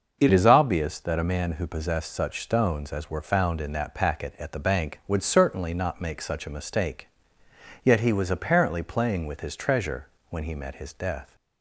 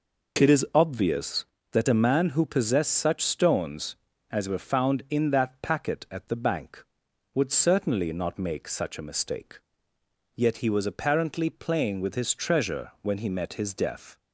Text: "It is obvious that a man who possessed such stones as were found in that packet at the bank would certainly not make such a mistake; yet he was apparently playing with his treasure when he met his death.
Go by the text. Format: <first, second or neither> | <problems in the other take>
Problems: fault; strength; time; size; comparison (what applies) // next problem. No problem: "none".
second | changes voice at "is"; from 0.3 s on; 11.0 s long // pauses between "treasure" and "when"; slight; at 10.0 s; 0.22 s long